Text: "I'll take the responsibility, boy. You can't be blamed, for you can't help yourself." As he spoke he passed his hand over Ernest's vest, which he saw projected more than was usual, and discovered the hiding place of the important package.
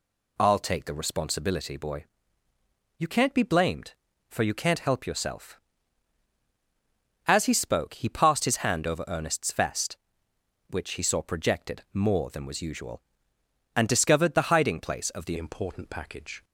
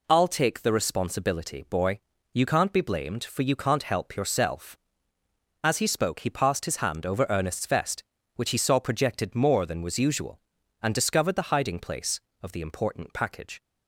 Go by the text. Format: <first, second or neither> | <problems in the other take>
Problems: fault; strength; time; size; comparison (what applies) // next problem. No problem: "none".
second | changes voice at "important"; from 15.3 s on; 1.1 s long